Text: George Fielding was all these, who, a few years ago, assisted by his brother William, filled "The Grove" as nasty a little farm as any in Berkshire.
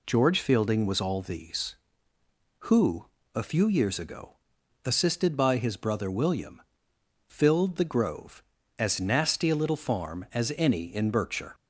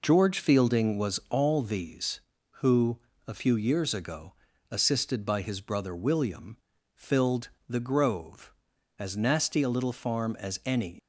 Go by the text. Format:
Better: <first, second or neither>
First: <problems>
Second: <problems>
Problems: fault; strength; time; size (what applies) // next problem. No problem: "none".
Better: first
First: none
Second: pauses between "filled" and "The"; slight; at 7.4 s; 0.20 s long // stops before "in Berkshire"; at 10.9 s